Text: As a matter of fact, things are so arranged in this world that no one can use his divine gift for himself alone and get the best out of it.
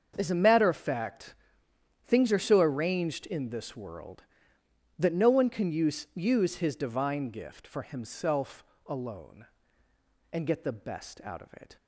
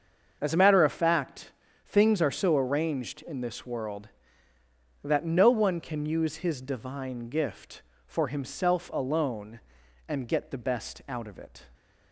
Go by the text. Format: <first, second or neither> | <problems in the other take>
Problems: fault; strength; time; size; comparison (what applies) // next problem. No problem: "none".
second | starts louder than the rest; until 1.1 s; 7 dB; also in the second // says "use" twice; at 6.1 s // pauses between "himself" and "alone"; slight; at 8.6 s; 0.24 s long